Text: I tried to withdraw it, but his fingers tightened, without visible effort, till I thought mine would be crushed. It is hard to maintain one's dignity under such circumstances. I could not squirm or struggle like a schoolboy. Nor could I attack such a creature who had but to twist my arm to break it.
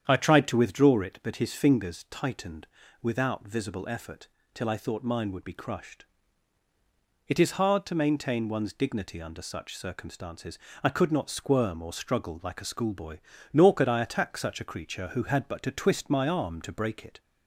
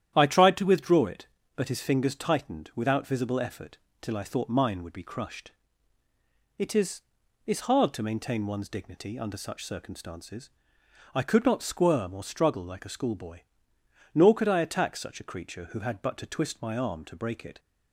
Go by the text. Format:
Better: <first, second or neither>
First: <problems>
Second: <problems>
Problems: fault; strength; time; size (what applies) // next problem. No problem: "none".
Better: first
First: starts louder than the rest; strong; until 1.0 s; 8.5 dB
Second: starts louder than the rest; strong; until 1.1 s; 10.5 dB // says "is" twice; at 7.4 s